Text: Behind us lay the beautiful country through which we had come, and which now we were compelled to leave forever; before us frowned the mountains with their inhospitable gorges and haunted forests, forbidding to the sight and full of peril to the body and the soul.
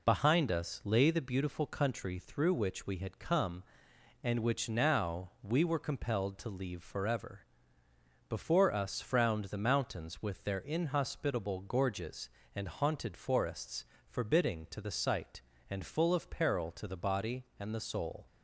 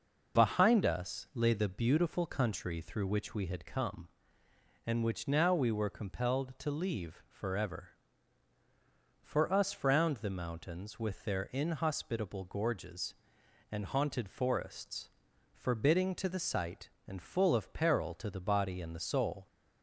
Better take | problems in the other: first | says "for" for "before"; at 9.2 s

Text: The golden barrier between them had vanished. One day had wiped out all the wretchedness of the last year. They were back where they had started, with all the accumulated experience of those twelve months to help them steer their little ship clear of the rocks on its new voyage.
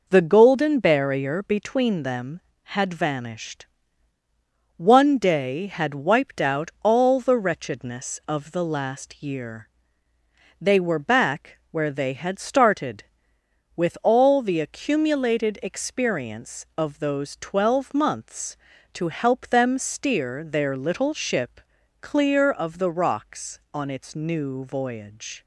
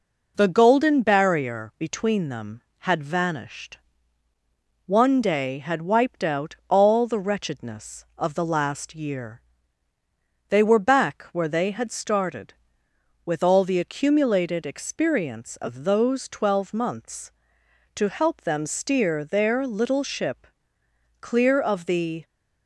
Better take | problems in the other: first | pauses between "ship" and "clear"; noticeable; at 20.4 s; 0.72 s long; also in the first // stops before "rocks on its new voyage"; at 22.2 s

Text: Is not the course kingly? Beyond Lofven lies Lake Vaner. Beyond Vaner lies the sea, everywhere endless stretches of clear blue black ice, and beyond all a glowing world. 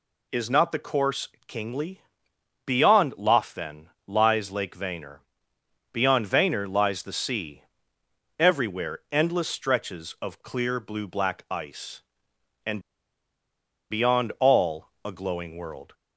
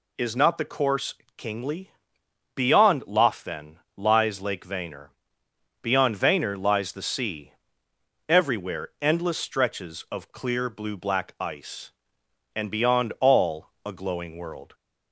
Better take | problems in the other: second | pauses between "course" and "kingly"; slight; at 1.2 s; 0.22 s long; slight in the second // pauses between "Lofven" and "lies"; slight; at 3.8 s; 0.20 s long; slight in the second // pauses between "and" and "beyond"; at 12.8 s; 1.1 s long // pauses between "all" and "a"; slight; at 14.8 s; 0.16 s long; slight in the second

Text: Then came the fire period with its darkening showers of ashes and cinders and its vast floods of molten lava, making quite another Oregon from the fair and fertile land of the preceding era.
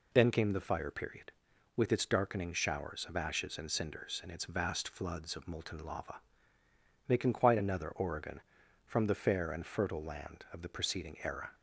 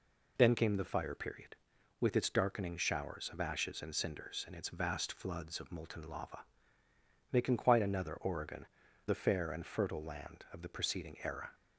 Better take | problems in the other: first | skips "from"; at 8.8 s

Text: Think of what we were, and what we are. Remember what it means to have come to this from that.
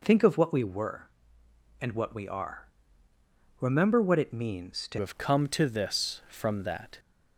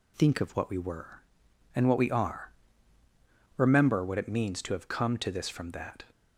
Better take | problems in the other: second | changes voice at "have"; from 4.9 s on; 2.0 s long

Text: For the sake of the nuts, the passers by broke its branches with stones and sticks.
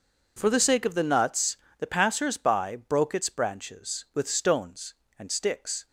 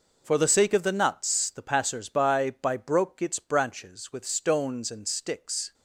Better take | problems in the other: first | says "by" twice; at 2.5 s

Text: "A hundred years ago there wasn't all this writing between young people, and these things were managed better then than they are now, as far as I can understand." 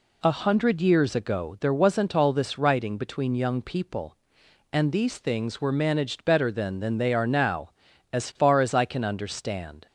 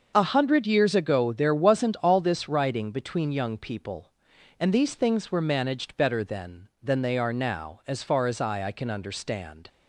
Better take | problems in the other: first | starts louder than the rest; until 1.1 s; 6.5 dB // says "I" twice; at 8.6 s

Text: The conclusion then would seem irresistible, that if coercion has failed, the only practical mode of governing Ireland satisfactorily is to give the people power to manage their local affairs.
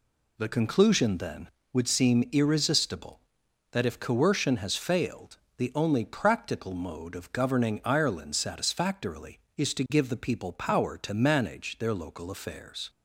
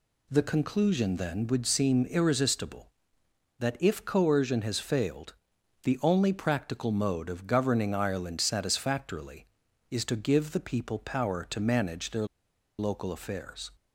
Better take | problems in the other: first | pauses between "their" and "local"; noticeable; at 12.2 s; 0.53 s long

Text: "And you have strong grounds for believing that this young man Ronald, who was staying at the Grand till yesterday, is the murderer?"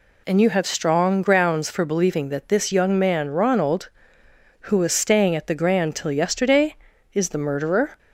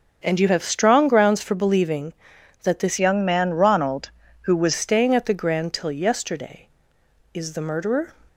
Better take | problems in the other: first | starts louder than the rest; until 1.2 s; 7 dB // changes voice from "young" to "was"; from 2.9 to 4.7 s; 1.8 s long

